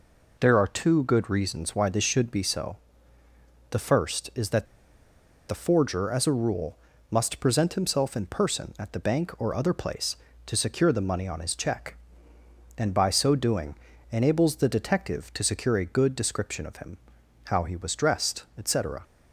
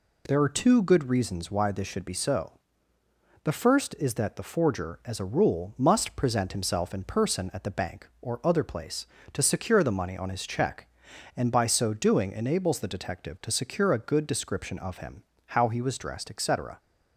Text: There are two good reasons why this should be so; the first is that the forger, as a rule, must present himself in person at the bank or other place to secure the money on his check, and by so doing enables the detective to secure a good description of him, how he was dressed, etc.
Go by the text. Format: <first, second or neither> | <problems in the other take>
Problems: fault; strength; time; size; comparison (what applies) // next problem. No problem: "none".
second | pauses between "that" and "the"; noticeable; at 4.6 s; 0.83 s long // pauses between "doing" and "enables"; slight; at 13.7 s; 0.36 s long